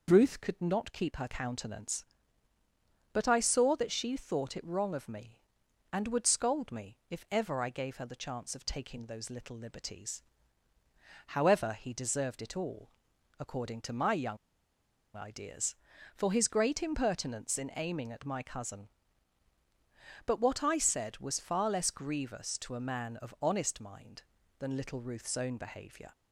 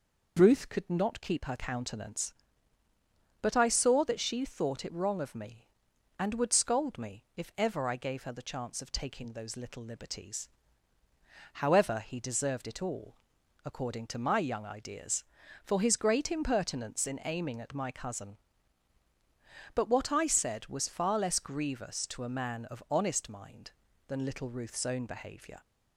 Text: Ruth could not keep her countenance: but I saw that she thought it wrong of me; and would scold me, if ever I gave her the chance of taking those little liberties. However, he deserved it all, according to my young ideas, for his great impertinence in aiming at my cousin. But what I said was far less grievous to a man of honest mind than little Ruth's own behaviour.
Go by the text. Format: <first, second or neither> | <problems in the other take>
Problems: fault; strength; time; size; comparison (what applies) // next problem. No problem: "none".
second | pauses between "young" and "ideas"; noticeable; at 14.3 s; 0.78 s long